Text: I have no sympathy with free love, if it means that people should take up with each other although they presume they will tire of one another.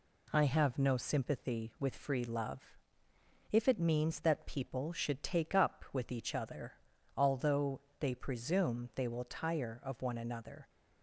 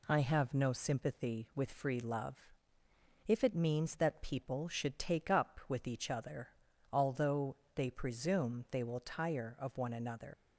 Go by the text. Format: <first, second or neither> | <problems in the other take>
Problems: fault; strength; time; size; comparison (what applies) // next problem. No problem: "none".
first | pauses between "other" and "although"; at 6.4 s; 0.44 s long; also in the first // pauses between "although" and "they"; slight; at 7.5 s; 0.18 s long; slight in the first // leaves "another" unfinished; at 10.3 s; 105 ms